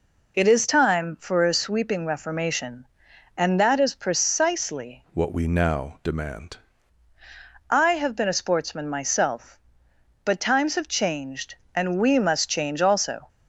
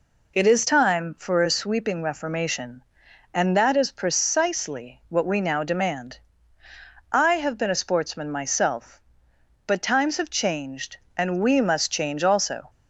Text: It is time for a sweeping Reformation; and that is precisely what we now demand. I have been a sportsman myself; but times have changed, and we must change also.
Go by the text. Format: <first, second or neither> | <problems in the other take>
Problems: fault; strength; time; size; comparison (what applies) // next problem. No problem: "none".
second | changes voice from "what" to "demand"; from 5.1 to 6.5 s; 1.4 s long